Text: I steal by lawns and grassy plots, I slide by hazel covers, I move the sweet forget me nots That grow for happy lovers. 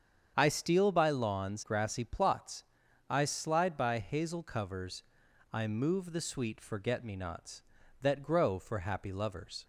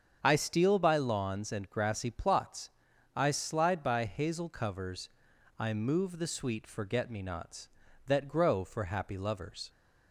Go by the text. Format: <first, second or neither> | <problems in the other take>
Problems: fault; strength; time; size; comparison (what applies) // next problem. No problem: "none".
second | starts louder than the rest; strong; until 1.3 s; 7.5 dB; strong in the second // skips "and"; at 1.6 s